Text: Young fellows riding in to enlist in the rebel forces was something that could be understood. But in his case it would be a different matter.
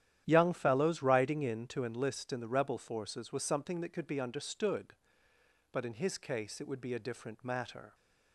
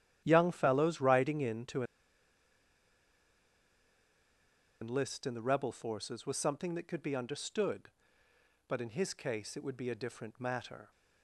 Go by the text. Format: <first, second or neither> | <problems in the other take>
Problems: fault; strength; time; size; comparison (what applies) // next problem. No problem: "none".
first | starts louder than the rest; strong; until 1.2 s; 11 dB; strong in the first // pauses between "to" and "enlist"; strong; at 1.8 s; 2.9 s long